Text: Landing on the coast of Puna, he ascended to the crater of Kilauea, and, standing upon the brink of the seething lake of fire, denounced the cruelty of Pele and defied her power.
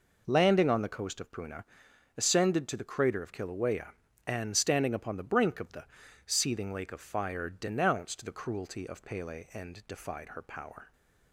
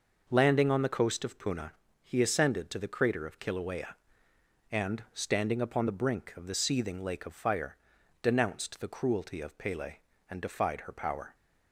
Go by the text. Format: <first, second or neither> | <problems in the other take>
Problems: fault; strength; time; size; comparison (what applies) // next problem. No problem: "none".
second | skips "he"; at 1.9 s // pauses between "the" and "seething"; at 5.8 s; 0.42 s long